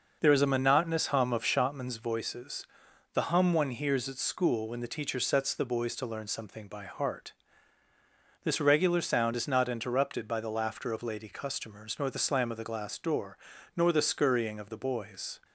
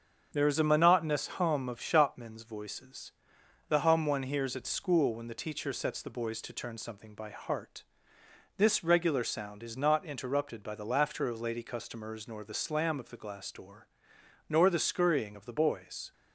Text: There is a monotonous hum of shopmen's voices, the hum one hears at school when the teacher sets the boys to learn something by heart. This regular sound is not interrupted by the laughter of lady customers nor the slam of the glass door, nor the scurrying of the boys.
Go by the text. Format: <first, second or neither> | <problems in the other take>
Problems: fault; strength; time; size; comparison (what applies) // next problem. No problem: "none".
first | starts louder than the rest; until 1.3 s; 7 dB // says "turn" for "learn"; at 6.5 s